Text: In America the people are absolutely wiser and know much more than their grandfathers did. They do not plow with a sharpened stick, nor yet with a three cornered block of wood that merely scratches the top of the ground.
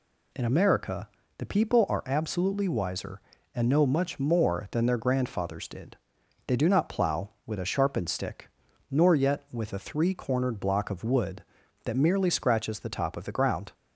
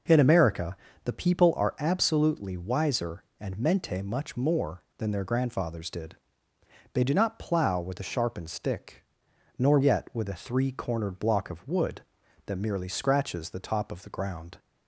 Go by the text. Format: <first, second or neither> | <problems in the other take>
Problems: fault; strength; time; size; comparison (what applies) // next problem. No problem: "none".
first | pauses between "America" and "the"; slight; at 0.7 s; 0.26 s long; slight in the first // says "mente" for "know"; at 3.5 s